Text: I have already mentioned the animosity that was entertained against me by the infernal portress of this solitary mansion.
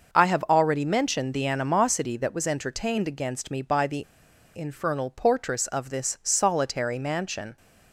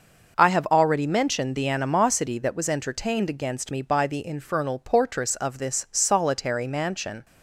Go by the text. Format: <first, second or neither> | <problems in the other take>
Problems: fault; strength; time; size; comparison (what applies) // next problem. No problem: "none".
second | starts louder than the rest; noticeable; until 1.1 s; 6 dB; noticeable in the second // pauses between "the" and "infernal"; noticeable; at 4.0 s; 0.52 s long